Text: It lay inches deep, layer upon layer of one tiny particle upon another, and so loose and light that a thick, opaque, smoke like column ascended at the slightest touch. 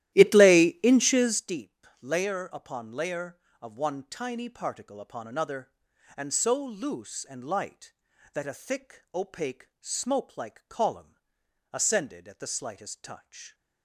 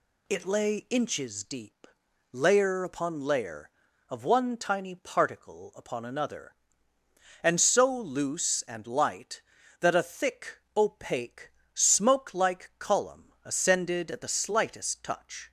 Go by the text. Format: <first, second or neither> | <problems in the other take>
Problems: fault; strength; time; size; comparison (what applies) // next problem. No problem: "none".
second | starts louder than the rest; strong; until 1.5 s; 13.5 dB // pauses between "column" and "ascended"; noticeable; at 11.1 s; 0.58 s long